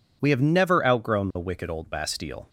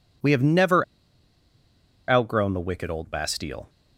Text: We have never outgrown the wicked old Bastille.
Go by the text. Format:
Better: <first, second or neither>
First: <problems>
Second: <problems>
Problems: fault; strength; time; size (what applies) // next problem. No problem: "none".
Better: first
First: none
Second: pauses between "never" and "outgrown"; strong; at 0.8 s; 1.2 s long